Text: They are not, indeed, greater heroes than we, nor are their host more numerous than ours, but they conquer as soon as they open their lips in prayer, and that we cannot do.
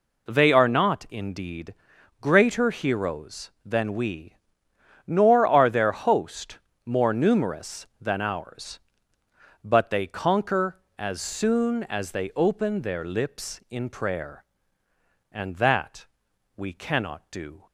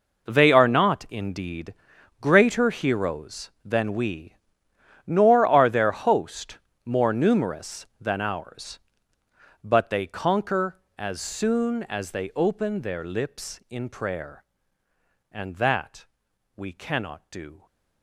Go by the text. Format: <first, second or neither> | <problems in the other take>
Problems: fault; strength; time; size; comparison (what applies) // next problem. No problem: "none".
first | gets quieter; strong; throughout; 14 dB // pauses between "host" and "more"; slight; at 6.5 s; 0.26 s long; slight in the first // pauses between "that" and "we"; noticeable; at 16.0 s; 0.50 s long; noticeable in the first